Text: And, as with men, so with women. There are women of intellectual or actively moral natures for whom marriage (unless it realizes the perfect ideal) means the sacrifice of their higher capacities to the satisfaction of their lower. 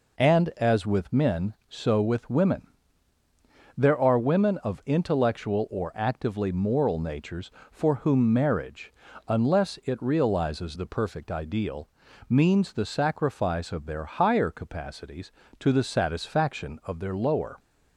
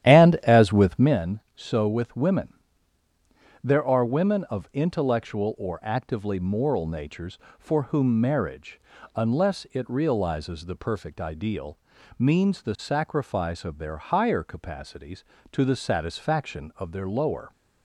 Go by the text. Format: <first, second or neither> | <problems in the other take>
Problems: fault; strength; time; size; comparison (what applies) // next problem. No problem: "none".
first | starts louder than the rest; strong; until 1.2 s; 11.5 dB